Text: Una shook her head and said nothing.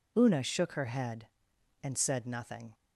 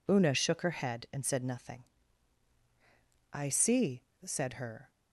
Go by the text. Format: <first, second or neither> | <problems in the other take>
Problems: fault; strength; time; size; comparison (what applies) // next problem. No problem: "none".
first | goes on to say "I see said her"; from 3.3 s on; 1.5 s long